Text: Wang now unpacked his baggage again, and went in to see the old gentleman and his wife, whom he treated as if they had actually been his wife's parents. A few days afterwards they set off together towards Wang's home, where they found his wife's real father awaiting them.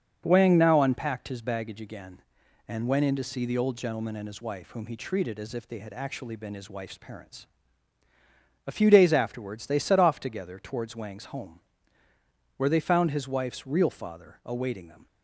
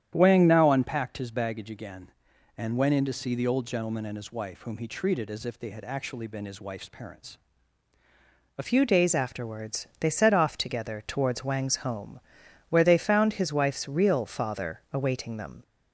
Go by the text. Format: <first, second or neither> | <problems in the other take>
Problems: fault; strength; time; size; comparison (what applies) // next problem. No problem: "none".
first | starts louder than the rest; strong; until 1.1 s; 10 dB; also in the first // changes voice at "few"; from 8.6 s on; 7.0 s long